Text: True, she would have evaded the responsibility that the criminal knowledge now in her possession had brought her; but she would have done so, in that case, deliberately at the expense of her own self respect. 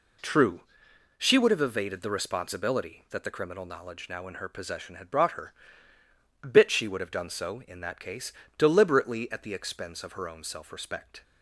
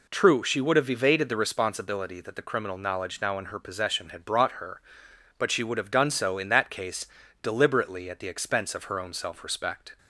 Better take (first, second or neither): second